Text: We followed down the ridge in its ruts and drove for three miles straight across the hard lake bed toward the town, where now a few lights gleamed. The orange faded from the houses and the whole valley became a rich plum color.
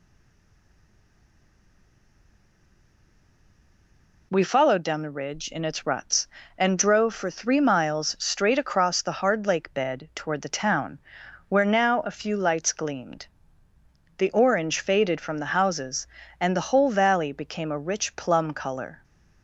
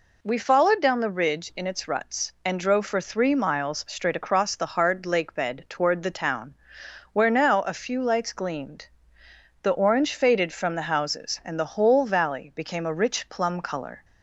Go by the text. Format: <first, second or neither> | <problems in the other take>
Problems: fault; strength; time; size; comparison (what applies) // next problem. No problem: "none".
second | stays silent before the first word; strong; until 4.3 s; 4.3 s long